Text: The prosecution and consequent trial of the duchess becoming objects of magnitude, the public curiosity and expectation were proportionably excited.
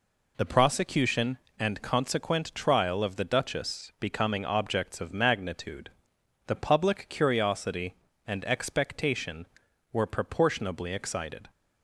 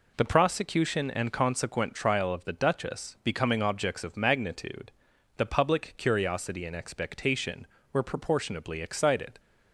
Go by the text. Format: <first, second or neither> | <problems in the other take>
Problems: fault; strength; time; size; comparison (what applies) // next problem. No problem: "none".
neither | none